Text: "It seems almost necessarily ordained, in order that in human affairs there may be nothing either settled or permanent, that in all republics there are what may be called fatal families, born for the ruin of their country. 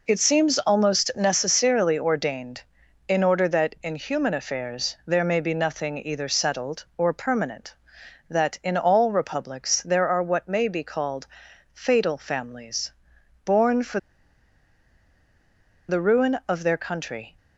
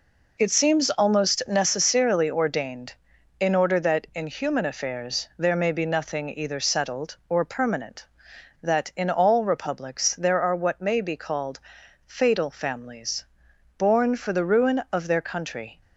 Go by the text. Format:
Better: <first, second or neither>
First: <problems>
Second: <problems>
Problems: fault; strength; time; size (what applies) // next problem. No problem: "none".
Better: second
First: pauses between "called" and "fatal"; noticeable; at 11.2 s; 0.48 s long // pauses between "for" and "the"; strong; at 13.9 s; 1.9 s long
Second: pauses between "called" and "fatal"; noticeable; at 11.5 s; 0.48 s long